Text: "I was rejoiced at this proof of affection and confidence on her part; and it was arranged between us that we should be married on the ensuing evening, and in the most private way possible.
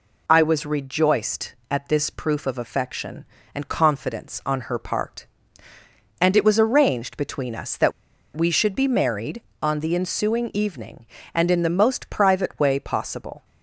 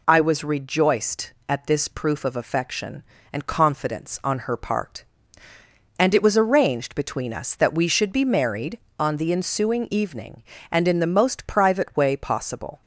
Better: second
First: pauses between "that" and "we"; at 7.9 s; 0.44 s long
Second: none

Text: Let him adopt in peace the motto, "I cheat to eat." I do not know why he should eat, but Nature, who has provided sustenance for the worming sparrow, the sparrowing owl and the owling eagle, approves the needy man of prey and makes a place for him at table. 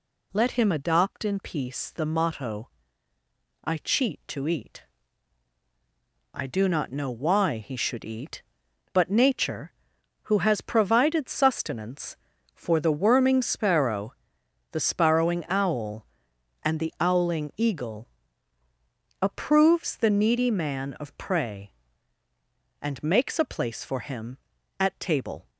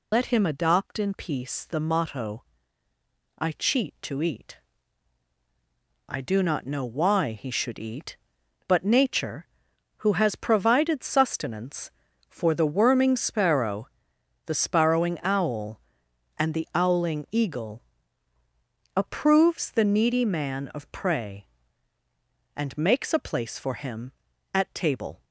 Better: first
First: none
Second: loses the start of "Let"; at 0.1 s; 60 ms

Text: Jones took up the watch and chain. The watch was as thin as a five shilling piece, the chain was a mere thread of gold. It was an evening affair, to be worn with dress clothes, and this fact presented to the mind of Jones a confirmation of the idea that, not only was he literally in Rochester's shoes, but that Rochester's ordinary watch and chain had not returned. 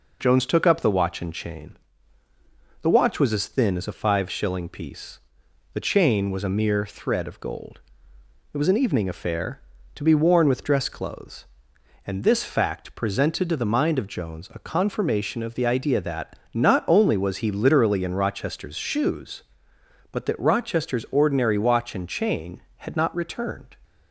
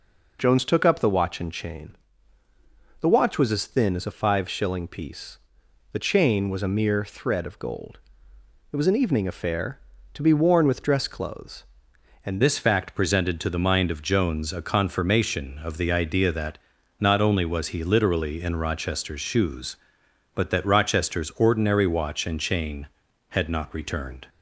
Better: first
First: none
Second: changes voice at "this"; from 12.4 s on; 11.8 s long

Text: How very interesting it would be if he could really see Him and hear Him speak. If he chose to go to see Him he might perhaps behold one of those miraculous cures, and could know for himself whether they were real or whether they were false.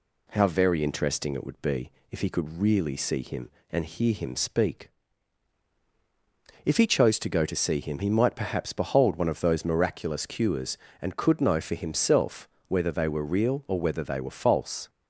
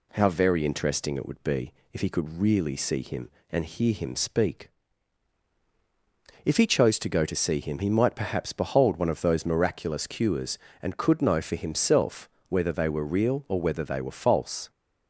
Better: neither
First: pauses between "be" and "if"; slight; at 1.9 s; 0.20 s long // pauses between "himself" and "whether"; slight; at 12.4 s; 0.20 s long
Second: pauses between "be" and "if"; slight; at 1.7 s; 0.20 s long // pauses between "himself" and "whether"; slight; at 12.2 s; 0.20 s long

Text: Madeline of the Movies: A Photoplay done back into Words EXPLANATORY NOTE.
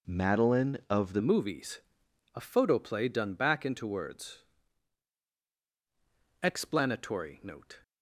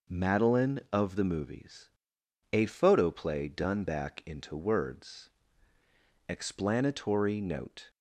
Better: second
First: changes voice at "Movies"; from 1.2 s on; 6.5 s long // pauses between "Words" and "EXPLANATORY"; strong; at 4.4 s; 2.0 s long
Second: pauses between "Words" and "EXPLANATORY"; noticeable; at 5.2 s; 0.98 s long

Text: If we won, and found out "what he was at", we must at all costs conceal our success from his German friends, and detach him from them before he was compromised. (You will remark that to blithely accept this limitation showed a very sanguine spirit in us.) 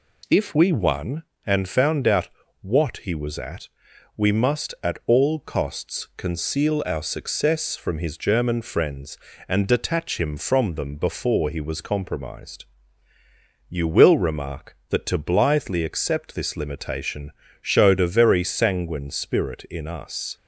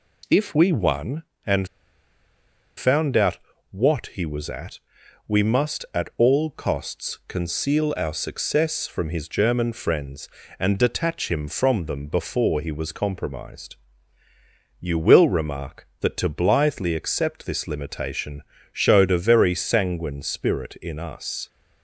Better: first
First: pauses between "out" and "what"; slight; at 2.2 s; 0.34 s long // pauses between "limitation" and "showed"; slight; at 17.3 s; 0.28 s long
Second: pauses between "and" and "found"; at 1.6 s; 1.1 s long // pauses between "out" and "what"; slight; at 3.3 s; 0.34 s long // pauses between "limitation" and "showed"; slight; at 18.4 s; 0.28 s long

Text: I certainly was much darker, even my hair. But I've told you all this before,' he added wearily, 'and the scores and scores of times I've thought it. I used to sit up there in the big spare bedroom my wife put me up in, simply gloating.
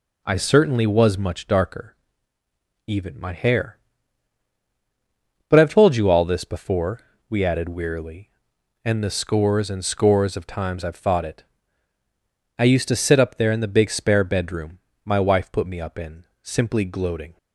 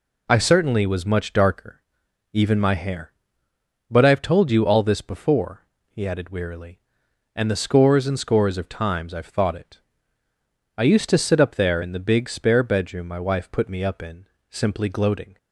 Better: second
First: says "we" for "he"; at 7.2 s // pauses between "bedroom" and "my"; slight; at 14.7 s; 0.26 s long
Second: none

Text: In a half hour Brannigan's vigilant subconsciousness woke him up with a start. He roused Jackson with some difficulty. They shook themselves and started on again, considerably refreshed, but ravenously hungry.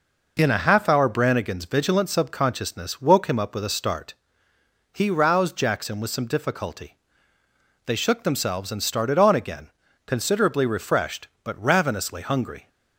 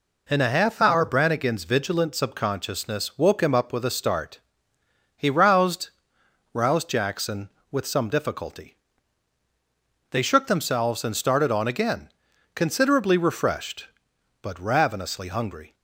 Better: first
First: none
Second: says "roused" twice; at 6.5 s

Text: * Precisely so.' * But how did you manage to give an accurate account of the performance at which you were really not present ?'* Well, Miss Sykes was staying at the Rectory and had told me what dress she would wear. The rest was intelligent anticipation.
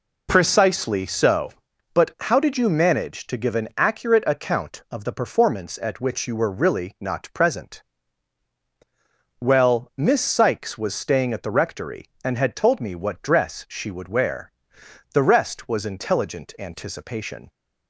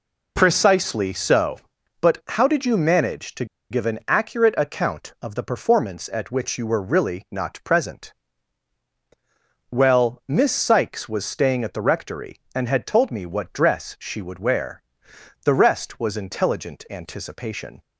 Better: first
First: none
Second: pauses between "to" and "give"; slight; at 3.4 s; 0.25 s long

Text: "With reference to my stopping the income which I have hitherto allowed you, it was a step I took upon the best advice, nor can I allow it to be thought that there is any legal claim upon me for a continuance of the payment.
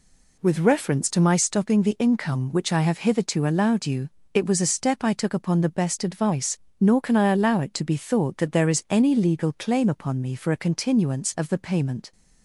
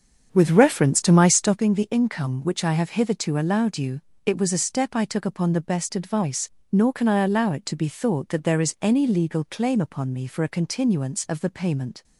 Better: first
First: none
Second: starts louder than the rest; strong; until 1.6 s; 7 dB

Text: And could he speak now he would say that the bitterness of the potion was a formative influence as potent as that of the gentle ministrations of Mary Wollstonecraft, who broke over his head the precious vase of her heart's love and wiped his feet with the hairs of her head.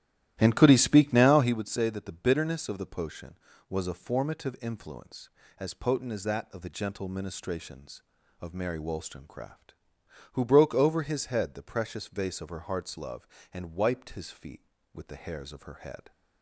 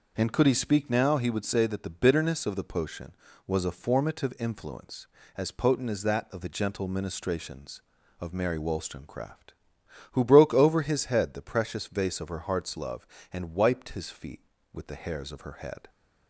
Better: second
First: starts louder than the rest; strong; until 1.6 s; 13.5 dB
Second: none

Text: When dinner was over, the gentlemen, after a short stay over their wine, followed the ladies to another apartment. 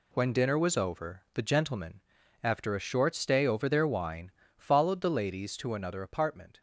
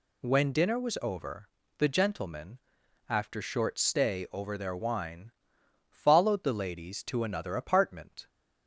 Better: first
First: none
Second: skips "a"; at 3.4 s

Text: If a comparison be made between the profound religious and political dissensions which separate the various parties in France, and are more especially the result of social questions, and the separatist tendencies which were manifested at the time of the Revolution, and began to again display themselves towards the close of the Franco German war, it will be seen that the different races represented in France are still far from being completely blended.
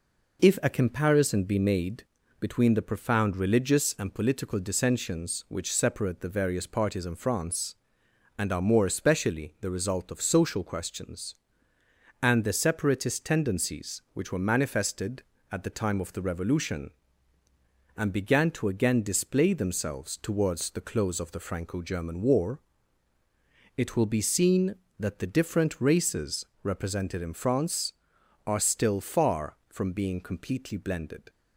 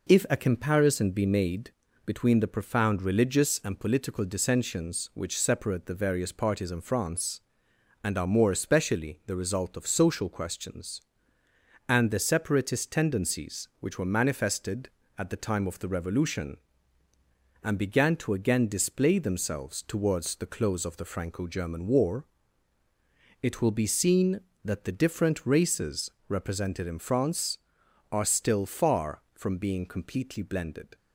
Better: neither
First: pauses between "made" and "between"; slight; at 2.0 s; 0.36 s long // pauses between "races" and "represented"; slight; at 26.4 s; 0.18 s long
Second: pauses between "made" and "between"; slight; at 1.7 s; 0.34 s long // pauses between "races" and "represented"; slight; at 26.1 s; 0.18 s long

